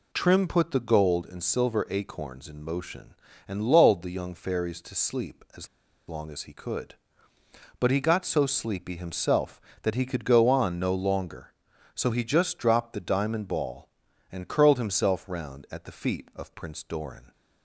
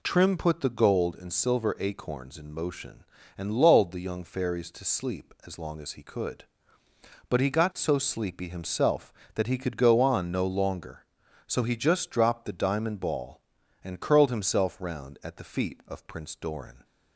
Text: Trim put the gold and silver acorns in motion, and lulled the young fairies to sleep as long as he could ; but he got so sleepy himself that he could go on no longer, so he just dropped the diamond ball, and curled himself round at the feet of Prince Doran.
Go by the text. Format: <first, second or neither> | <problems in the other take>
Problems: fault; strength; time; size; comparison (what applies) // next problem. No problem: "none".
second | pauses between "as" and "long"; at 5.6 s; 0.40 s long